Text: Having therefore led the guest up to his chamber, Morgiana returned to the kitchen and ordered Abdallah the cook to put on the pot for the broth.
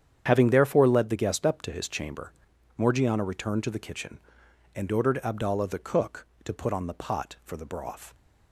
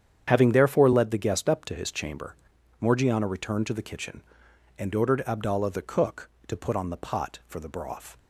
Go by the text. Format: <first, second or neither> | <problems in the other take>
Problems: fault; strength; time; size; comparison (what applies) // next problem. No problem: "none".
neither | starts louder than the rest; strong; the same in both